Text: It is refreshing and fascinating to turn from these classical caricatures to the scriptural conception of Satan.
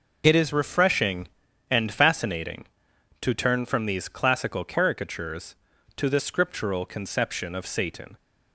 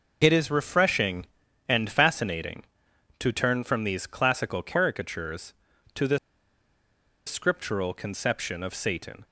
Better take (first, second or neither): first